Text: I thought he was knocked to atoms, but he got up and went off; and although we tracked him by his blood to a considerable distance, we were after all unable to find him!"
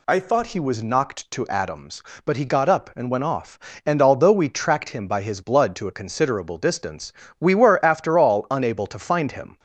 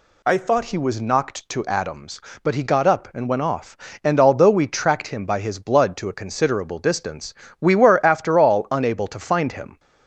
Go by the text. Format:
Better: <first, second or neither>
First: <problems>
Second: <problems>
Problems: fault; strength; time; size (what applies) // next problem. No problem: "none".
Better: neither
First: none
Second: none